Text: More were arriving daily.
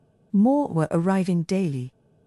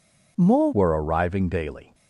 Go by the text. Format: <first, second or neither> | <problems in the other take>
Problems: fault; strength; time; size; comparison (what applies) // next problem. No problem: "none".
first | changes voice at "were"; from 0.7 s on; 1.2 s long